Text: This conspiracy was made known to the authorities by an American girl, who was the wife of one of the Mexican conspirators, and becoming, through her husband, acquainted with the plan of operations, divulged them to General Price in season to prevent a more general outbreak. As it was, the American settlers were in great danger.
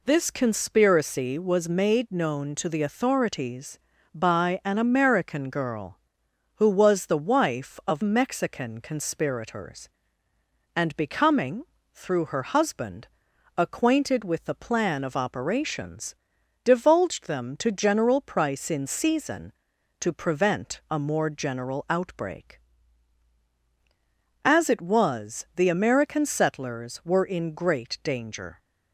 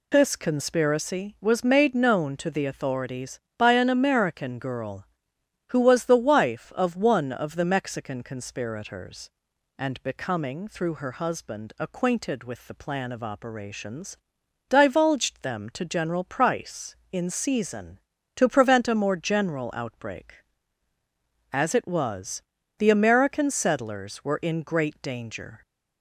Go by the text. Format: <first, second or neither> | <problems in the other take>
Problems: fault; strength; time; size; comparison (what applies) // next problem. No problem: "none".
second | skips "one of the"; at 8.0 s